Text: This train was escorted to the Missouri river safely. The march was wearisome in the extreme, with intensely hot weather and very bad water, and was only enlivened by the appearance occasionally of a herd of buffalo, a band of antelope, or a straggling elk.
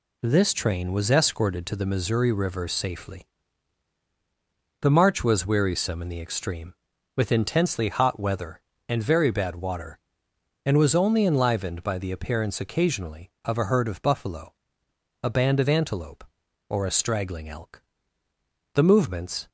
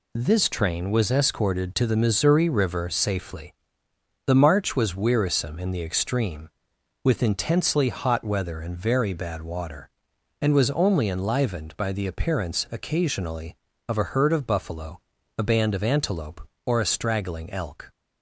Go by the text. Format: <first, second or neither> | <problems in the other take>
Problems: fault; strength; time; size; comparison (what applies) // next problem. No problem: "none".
second | goes on to say "The movements"; noticeable; from 18.7 s on; 0.74 s long